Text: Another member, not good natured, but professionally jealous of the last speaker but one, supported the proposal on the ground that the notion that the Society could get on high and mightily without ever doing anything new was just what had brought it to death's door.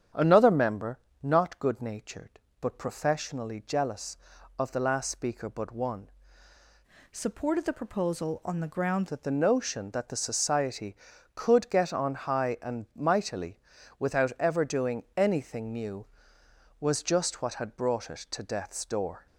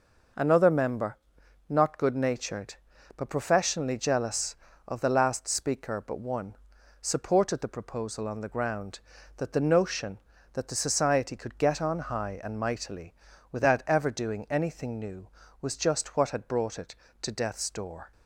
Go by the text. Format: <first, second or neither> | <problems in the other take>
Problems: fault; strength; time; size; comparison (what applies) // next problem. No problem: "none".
second | starts louder than the rest; strong; until 1.3 s; 9 dB // changes voice from "supported" to "ground"; from 7.1 to 9.0 s; 1.9 s long // pauses between "mightily" and "without"; at 13.6 s; 0.40 s long; also in the second